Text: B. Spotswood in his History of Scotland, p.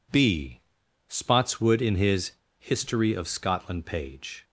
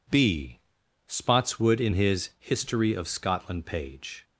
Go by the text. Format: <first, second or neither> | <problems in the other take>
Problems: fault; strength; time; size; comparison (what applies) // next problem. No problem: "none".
second | pauses between "his" and "History"; slight; at 2.3 s; 0.26 s long